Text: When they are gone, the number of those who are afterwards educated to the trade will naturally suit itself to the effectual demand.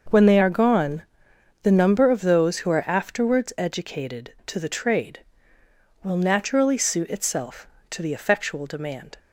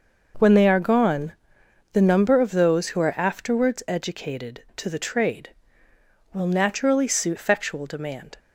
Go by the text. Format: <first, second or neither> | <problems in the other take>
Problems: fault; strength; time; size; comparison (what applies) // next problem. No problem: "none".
first | skips "itself to the"; at 7.3 s